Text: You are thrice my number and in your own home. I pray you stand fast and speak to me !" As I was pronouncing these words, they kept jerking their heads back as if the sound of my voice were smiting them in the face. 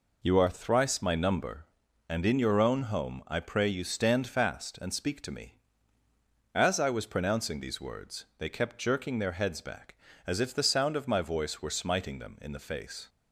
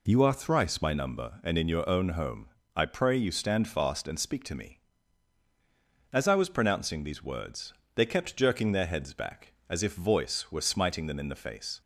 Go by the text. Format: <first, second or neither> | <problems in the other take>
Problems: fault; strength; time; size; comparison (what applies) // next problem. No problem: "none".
first | skips "the sound of my"; at 9.9 s